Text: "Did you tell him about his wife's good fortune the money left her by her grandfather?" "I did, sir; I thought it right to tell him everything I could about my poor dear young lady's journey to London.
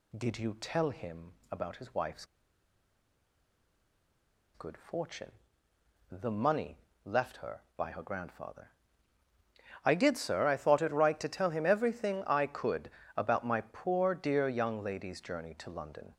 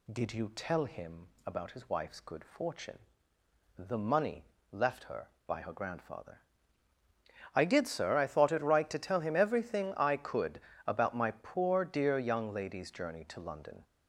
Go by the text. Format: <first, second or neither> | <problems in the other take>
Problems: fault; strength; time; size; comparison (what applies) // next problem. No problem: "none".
second | pauses between "him" and "about"; slight; at 1.3 s; 0.18 s long; slight in the second // pauses between "wife's" and "good"; strong; at 2.2 s; 2.2 s long // pauses between "fortune" and "the"; noticeable; at 5.3 s; 0.80 s long; noticeable in the second // pauses between "money" and "left"; slight; at 6.7 s; 0.26 s long; slight in the second // pauses between "could" and "about"; slight; at 12.9 s; 0.24 s long; slight in the second